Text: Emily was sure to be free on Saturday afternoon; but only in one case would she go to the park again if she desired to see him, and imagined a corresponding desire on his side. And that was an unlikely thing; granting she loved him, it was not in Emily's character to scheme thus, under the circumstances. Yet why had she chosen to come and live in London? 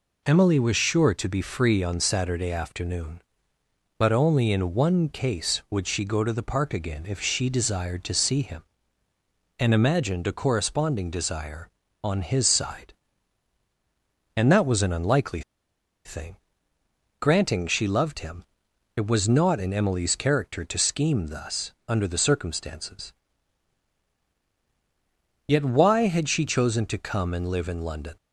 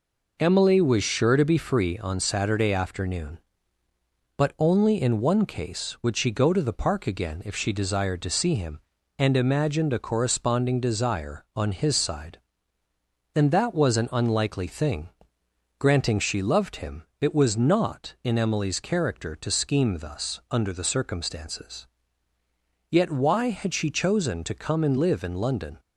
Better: second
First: pauses between "unlikely" and "thing"; noticeable; at 15.4 s; 0.64 s long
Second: none

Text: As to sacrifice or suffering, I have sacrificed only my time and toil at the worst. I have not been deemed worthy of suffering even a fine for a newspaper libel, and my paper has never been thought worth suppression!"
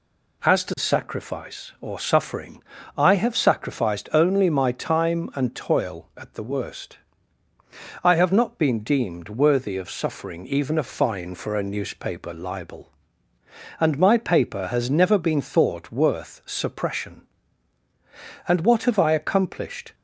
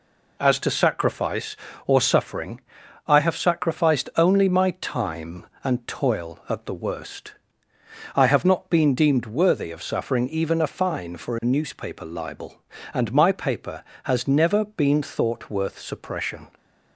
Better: second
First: goes on to say "And what have I accomplished"; from 18.4 s on; 1.4 s long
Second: none

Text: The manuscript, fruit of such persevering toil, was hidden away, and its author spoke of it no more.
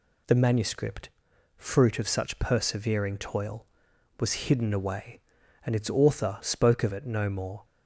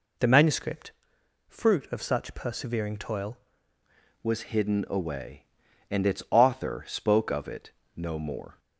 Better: first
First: none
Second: changes voice at "was"; from 4.2 s on; 4.3 s long // pauses between "it" and "no"; slight; at 7.7 s; 0.24 s long

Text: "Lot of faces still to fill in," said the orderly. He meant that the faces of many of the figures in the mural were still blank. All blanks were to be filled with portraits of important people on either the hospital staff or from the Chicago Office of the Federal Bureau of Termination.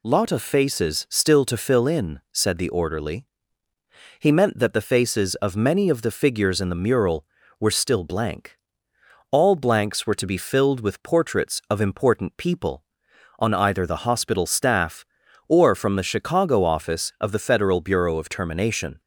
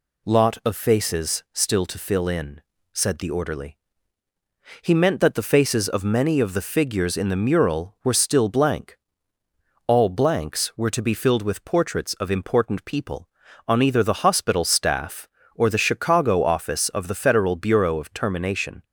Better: first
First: none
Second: skips "from"; at 15.7 s

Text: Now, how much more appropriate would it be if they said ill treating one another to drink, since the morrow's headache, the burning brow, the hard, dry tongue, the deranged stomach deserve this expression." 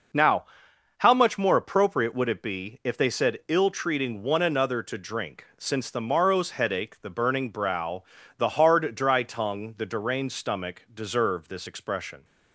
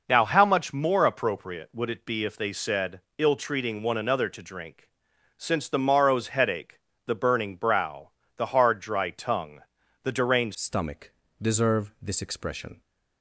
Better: first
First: none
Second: pauses between "said" and "ill"; slight; at 3.0 s; 0.16 s long // changes voice at "stomach"; from 10.5 s on; 2.3 s long // pauses between "stomach" and "deserve"; slight; at 11.1 s; 0.28 s long

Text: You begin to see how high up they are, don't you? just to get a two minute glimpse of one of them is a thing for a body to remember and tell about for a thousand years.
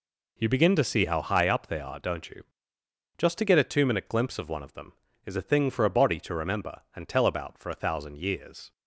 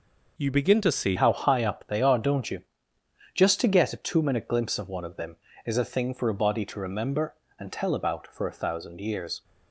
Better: first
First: none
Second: changes voice at "how"; from 1.1 s on; 8.3 s long

